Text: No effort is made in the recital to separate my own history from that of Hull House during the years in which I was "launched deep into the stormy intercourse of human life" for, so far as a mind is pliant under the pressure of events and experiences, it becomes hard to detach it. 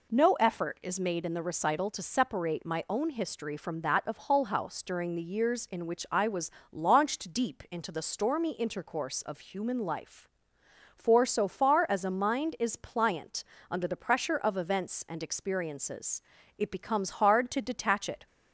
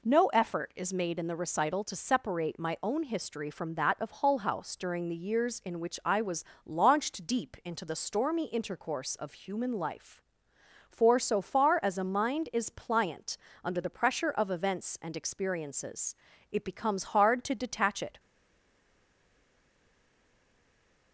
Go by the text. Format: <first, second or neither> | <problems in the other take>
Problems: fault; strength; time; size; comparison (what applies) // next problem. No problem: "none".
first | pauses between "was" and "launched"; slight; at 6.4 s; 0.22 s long; slight in the first // pauses between "pliant" and "under"; slight; at 13.3 s; 0.26 s long; slight in the first // stays silent after the last word; strong; from 18.1 s on; 3.0 s long